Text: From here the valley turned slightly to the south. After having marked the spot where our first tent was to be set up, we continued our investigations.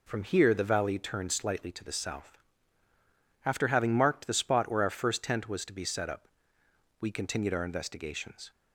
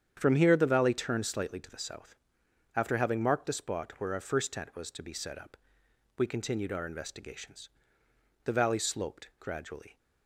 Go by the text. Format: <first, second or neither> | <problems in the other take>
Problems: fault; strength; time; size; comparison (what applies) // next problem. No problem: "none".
first | starts louder than the rest; strong; until 1.1 s; 8.5 dB // goes on to say "The valley sloped gradually"; from 8.4 s on; 1.5 s long